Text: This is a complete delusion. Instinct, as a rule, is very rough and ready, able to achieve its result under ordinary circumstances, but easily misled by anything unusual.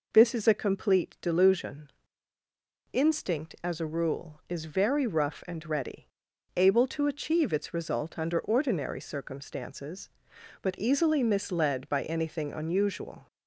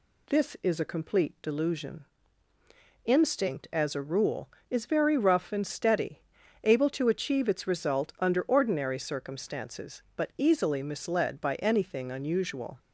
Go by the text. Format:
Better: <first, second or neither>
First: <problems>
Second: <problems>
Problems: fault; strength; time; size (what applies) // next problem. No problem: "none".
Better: first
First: none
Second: says "steady" for "ready"; at 5.6 s